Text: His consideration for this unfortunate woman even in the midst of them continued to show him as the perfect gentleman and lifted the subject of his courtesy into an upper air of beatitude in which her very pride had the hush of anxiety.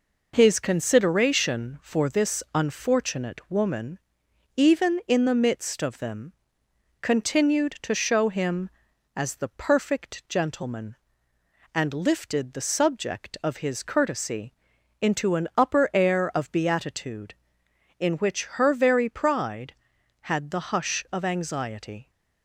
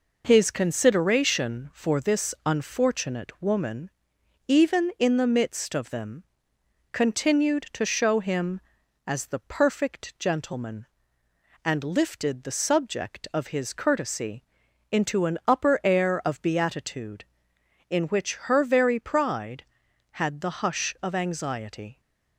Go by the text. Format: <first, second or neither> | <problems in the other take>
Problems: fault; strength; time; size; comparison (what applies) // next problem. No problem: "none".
neither | pauses between "woman" and "even"; noticeable; the same in both // pauses between "them" and "continued"; noticeable; the same in both // pauses between "courtesy" and "into"; noticeable; the same in both